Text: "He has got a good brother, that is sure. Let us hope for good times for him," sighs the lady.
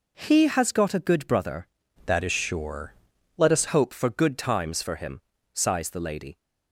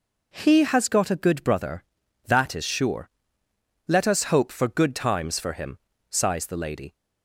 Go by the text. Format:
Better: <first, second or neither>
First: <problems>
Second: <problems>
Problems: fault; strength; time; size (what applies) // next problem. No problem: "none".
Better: second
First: changes voice from "that" to "us"; from 2.0 to 3.6 s; 1.6 s long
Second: none